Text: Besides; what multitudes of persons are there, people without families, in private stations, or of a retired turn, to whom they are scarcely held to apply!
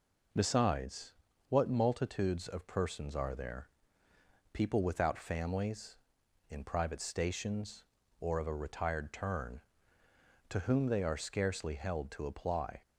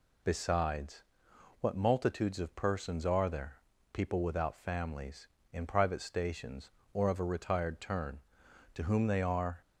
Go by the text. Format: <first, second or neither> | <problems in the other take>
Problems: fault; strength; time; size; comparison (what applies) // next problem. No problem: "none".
first | stops before "scarcely held to apply"; at 9.6 s